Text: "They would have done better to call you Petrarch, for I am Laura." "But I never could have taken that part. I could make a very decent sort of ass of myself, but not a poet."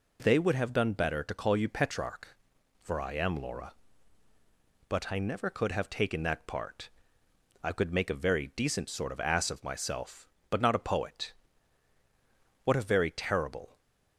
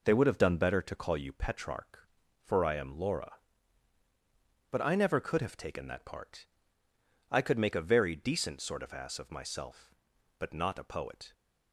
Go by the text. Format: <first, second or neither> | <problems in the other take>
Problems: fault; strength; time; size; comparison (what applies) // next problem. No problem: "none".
second | goes on to say "What a very terrible"; noticeable; from 12.6 s on; 1.1 s long